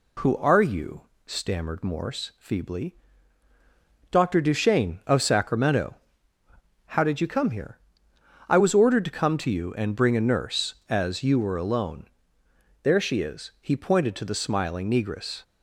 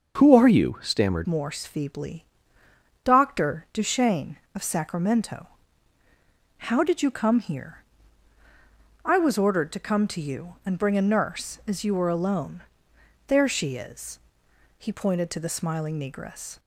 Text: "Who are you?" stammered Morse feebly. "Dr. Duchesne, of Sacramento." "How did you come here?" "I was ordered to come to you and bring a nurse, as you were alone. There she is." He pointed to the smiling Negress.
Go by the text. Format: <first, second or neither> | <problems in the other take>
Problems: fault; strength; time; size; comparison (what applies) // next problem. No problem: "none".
first | starts louder than the rest; until 1.1 s; 6.5 dB // changes voice at "Morse"; from 1.2 s on; 15.3 s long